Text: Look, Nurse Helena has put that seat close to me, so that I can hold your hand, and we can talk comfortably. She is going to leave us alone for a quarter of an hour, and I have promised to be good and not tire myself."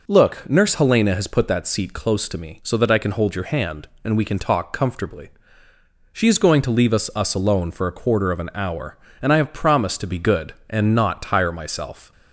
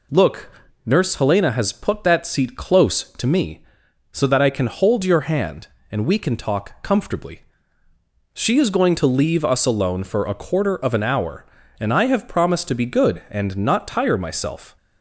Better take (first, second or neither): second